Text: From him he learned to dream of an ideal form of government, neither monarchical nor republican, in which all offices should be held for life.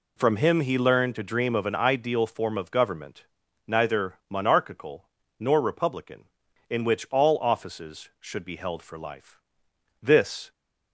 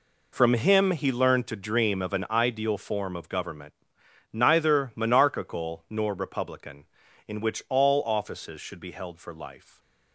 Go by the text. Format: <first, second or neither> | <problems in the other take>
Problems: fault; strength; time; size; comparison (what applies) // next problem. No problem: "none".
second | pauses between "monarchical" and "nor"; slight; at 5.0 s; 0.30 s long // goes on to say "This"; from 10.0 s on; 0.50 s long